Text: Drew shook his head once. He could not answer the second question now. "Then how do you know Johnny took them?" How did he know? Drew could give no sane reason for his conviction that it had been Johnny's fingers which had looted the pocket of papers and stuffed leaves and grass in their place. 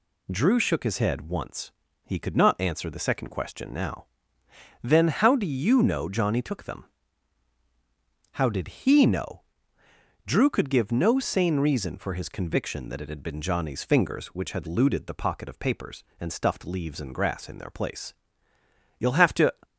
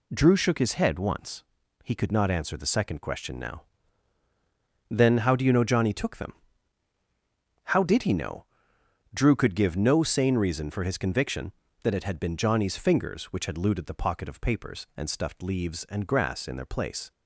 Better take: second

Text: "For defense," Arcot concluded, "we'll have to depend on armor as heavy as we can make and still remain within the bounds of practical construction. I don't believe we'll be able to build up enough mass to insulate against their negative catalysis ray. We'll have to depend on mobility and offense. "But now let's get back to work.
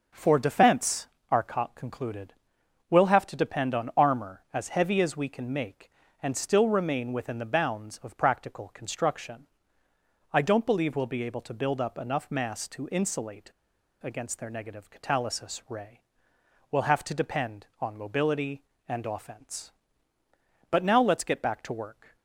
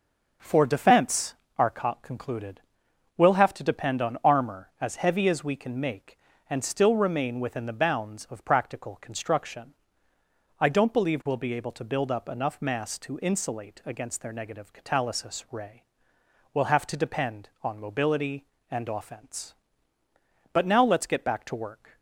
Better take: second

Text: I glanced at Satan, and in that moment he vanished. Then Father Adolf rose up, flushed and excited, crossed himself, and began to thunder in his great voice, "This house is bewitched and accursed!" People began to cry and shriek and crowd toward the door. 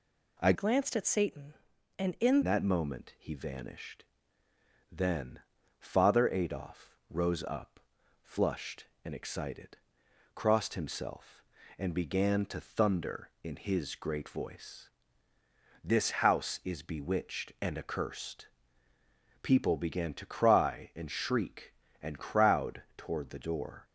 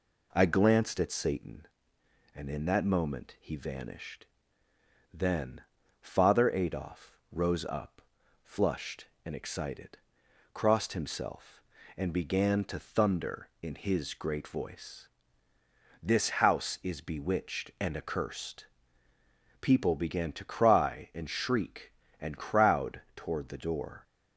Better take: second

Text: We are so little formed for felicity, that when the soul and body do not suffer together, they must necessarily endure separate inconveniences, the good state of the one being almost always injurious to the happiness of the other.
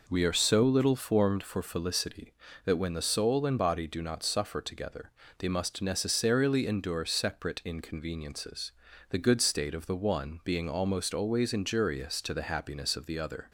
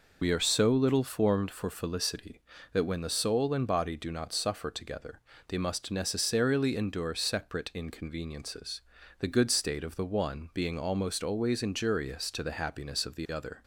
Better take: first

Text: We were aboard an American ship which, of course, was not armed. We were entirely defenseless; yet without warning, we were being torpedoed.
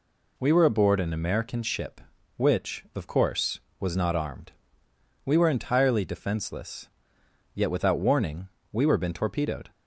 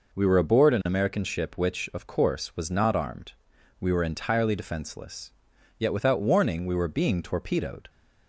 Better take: second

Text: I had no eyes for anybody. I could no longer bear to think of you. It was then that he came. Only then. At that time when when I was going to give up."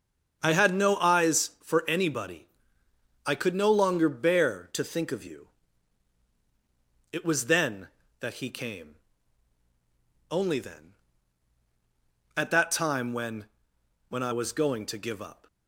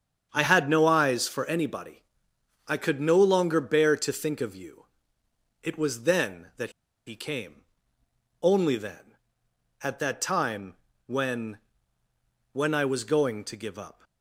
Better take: first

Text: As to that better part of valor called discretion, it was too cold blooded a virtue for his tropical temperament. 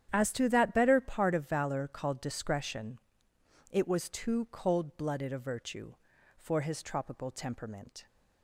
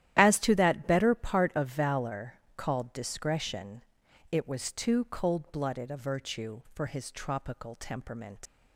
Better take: first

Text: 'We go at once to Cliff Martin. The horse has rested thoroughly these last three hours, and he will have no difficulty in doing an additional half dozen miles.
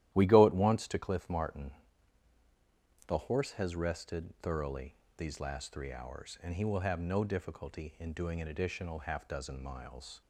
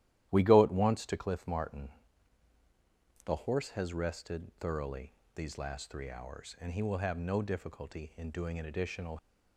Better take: first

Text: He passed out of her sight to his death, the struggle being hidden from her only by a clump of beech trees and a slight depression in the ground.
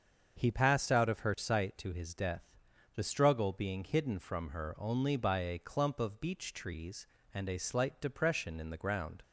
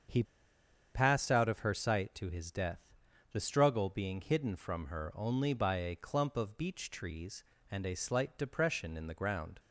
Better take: first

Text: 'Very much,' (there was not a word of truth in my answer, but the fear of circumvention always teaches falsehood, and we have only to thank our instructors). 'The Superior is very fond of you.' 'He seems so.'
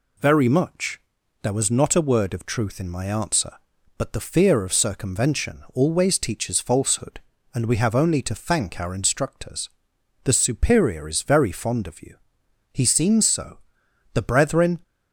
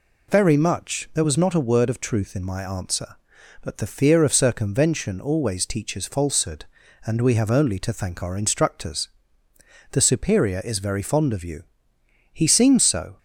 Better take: second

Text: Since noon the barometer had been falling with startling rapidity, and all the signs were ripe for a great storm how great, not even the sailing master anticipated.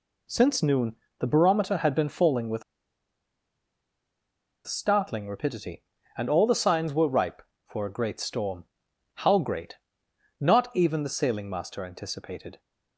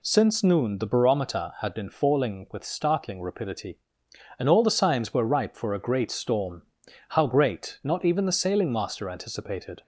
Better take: second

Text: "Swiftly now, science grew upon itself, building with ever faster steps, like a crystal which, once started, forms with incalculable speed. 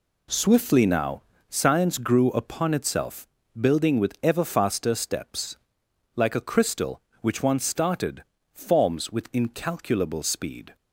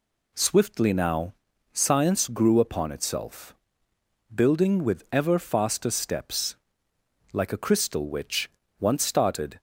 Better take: first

